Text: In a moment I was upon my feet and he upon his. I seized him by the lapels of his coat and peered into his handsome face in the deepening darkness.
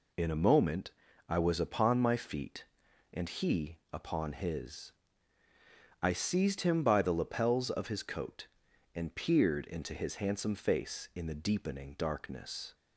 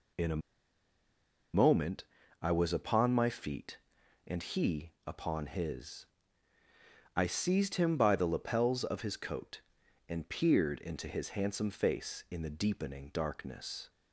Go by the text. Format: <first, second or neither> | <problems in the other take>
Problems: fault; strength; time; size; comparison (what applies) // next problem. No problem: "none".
first | pauses between "a" and "moment"; at 0.4 s; 1.1 s long // pauses between "moment" and "I"; slight; at 2.0 s; 0.36 s long; slight in the first // pauses between "he" and "upon"; slight; at 4.9 s; 0.16 s long; slight in the first